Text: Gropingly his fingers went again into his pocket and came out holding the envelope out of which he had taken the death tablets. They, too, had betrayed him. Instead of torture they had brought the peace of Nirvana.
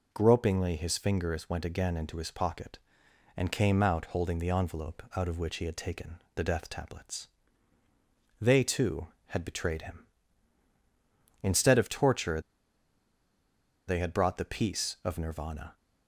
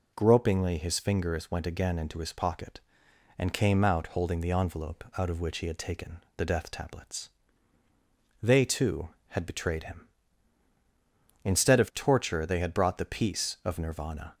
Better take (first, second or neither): second